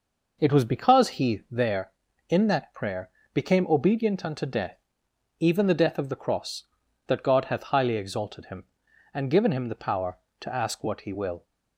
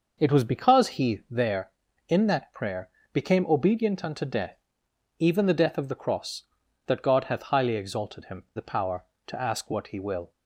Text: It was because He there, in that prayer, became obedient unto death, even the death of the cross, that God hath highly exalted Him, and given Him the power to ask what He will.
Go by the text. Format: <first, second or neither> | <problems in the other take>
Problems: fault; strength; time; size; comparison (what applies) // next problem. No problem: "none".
first | skips "and given Him"; at 8.4 s